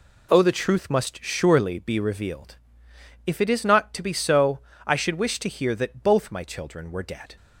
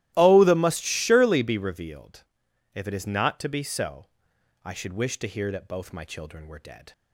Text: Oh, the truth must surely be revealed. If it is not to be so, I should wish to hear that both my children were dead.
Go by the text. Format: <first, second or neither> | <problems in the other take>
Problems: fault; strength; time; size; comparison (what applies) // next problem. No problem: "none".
first | starts louder than the rest; strong; until 1.1 s; 15 dB // skips "truth"; at 0.5 s